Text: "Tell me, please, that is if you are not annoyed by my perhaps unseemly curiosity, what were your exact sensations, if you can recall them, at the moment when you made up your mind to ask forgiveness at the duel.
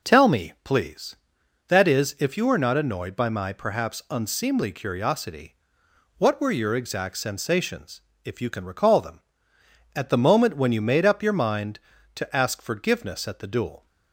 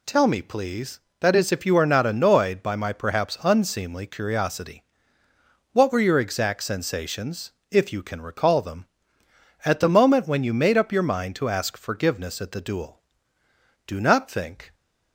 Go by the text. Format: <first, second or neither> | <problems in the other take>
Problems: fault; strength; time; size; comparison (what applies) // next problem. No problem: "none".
first | goes on to say "Do not think"; noticeable; from 13.8 s on; 0.88 s long